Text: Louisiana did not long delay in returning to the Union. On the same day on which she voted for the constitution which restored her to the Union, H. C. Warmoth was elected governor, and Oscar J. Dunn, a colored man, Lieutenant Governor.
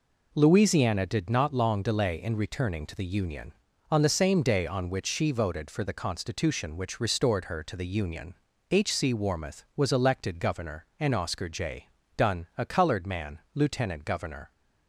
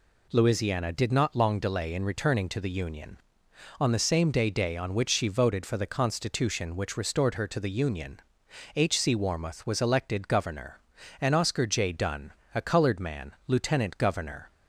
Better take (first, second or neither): first